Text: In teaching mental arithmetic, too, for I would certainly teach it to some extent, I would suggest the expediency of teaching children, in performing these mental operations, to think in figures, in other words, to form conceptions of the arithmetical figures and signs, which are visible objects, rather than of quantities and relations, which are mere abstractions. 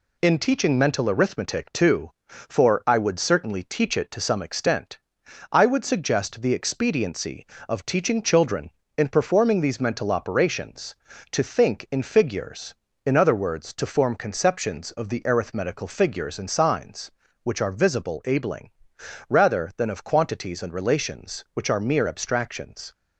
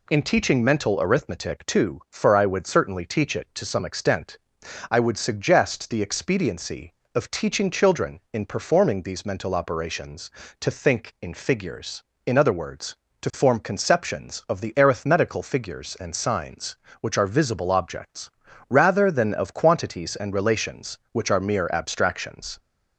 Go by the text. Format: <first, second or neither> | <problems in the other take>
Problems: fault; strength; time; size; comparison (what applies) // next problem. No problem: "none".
second | says "abling" for "objects"; at 18.2 s